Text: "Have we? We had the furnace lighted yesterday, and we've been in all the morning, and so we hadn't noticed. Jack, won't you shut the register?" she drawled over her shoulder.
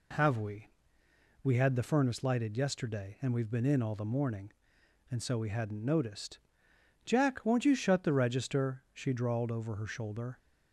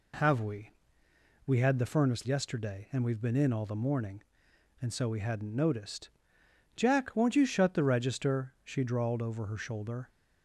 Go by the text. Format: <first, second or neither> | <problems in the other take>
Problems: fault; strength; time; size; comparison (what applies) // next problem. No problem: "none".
first | skips "lighted"; at 2.2 s